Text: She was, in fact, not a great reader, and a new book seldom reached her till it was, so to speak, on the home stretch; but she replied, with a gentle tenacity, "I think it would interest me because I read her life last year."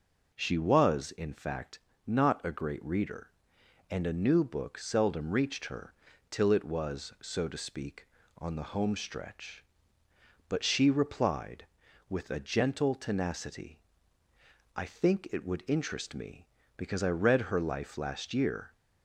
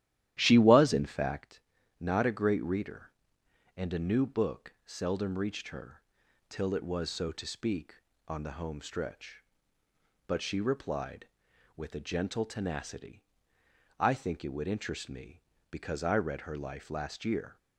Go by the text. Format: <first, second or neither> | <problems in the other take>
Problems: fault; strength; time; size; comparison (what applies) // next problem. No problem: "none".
first | starts louder than the rest; strong; until 1.4 s; 13 dB // pauses between "her" and "till"; noticeable; at 5.9 s; 0.48 s long; also in the first